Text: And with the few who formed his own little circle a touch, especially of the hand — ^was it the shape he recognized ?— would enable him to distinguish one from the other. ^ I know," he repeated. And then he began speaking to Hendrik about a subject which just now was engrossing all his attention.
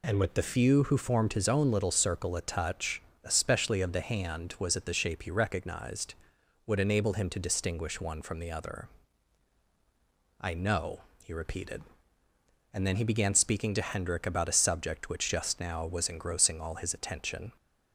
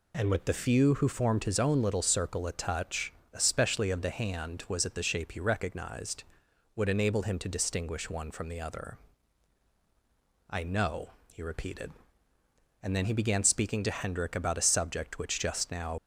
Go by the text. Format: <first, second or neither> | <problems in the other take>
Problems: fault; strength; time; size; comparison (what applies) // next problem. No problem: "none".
first | stops before "was engrossing all his attention"; at 15.9 s